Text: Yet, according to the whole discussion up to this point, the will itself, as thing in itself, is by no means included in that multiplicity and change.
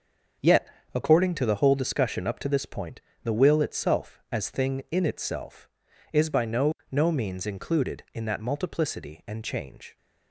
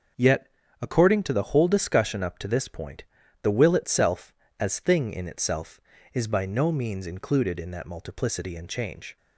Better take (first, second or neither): second